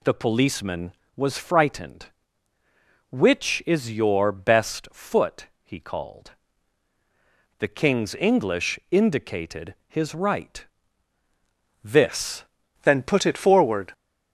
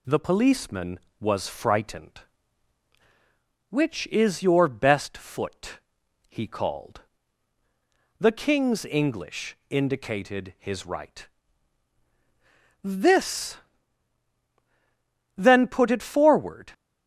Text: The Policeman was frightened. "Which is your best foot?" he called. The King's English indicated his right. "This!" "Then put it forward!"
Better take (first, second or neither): second